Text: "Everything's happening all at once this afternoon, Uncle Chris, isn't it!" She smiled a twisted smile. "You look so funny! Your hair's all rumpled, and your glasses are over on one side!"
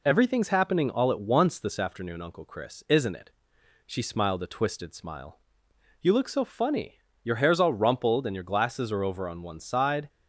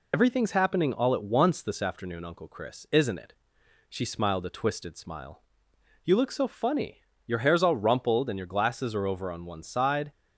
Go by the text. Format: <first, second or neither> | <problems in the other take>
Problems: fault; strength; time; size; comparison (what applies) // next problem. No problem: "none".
first | loses the start of "Everything's"; at 0.1 s; 65 ms